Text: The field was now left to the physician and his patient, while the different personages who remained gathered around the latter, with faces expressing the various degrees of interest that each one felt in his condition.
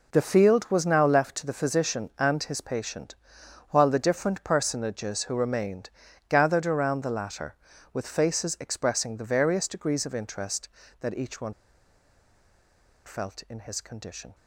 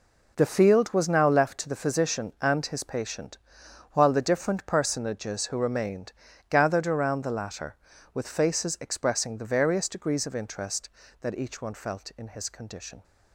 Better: second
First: pauses between "remained" and "gathered"; at 5.8 s; 0.40 s long // pauses between "one" and "felt"; strong; at 11.5 s; 1.5 s long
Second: pauses between "remained" and "gathered"; at 6.1 s; 0.38 s long

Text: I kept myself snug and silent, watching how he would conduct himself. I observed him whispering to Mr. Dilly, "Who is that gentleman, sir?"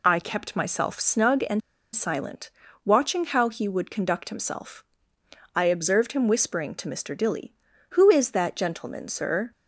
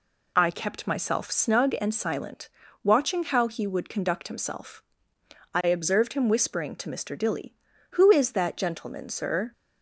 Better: second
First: pauses between "and" and "silent"; slight; at 1.6 s; 0.34 s long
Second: none

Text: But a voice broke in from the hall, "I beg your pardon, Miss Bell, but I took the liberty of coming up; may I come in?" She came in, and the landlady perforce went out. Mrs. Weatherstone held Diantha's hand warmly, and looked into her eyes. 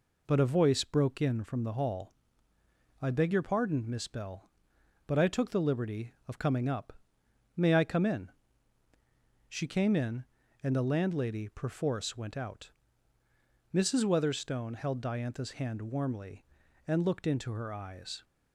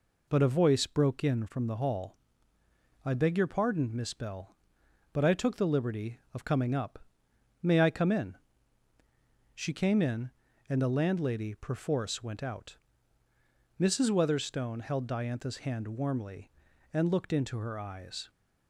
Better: neither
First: none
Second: none

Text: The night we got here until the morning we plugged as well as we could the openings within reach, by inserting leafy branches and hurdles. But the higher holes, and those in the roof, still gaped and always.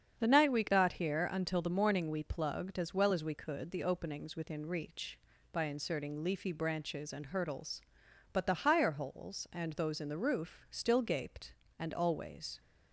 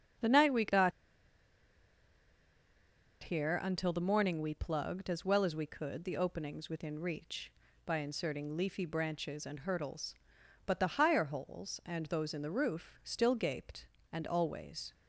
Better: first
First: starts louder than the rest; strong; until 1.1 s; 7.5 dB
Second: starts louder than the rest; strong; until 3.5 s; 7.5 dB // pauses between "got" and "here"; strong; at 0.9 s; 2.3 s long

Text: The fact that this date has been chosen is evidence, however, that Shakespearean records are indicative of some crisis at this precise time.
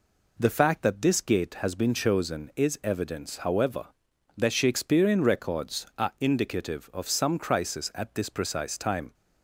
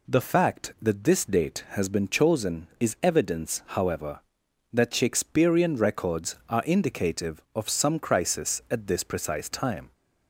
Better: second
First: says "gate" for "date"; at 1.1 s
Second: none

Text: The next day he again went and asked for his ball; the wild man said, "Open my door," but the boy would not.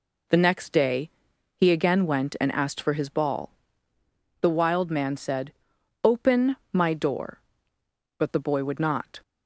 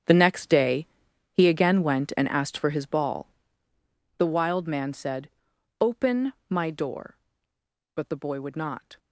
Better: first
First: pauses between "day" and "he"; noticeable; at 1.0 s; 0.46 s long // pauses between "Open" and "my"; slight; at 6.5 s; 0.16 s long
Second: gets quieter; strong; throughout; 14.5 dB // pauses between "day" and "he"; noticeable; at 0.8 s; 0.46 s long // pauses between "Open" and "my"; slight; at 6.3 s; 0.16 s long

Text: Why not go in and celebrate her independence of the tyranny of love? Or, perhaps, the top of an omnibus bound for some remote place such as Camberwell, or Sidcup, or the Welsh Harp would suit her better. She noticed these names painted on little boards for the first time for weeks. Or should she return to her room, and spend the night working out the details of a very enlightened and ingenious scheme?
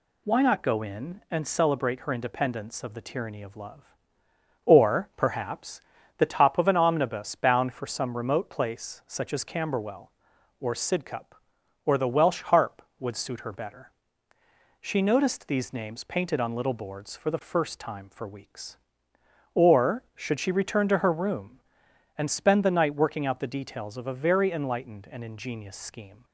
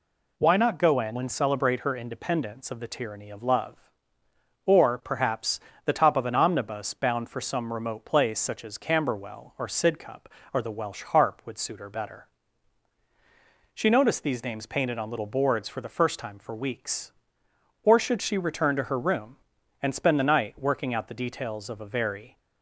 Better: first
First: none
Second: stops before "enlightened and ingenious scheme"; at 22.3 s

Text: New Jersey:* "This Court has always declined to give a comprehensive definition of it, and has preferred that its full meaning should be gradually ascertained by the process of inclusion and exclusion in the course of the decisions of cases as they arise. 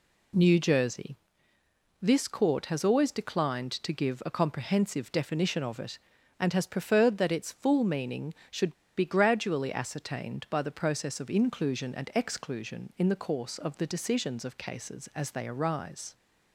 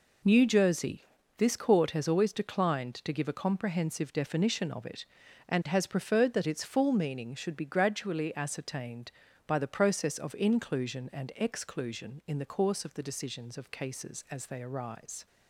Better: second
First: pauses between "should" and "be"; slight; at 8.7 s; 0.25 s long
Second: none

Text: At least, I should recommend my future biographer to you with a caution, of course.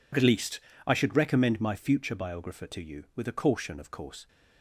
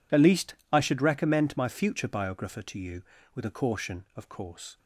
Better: neither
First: none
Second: none

